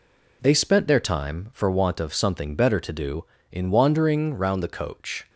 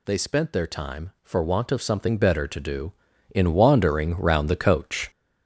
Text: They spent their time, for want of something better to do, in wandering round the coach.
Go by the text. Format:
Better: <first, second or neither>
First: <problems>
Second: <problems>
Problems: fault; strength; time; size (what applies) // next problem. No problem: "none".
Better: first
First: none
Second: gets louder; strong; throughout; 7 dB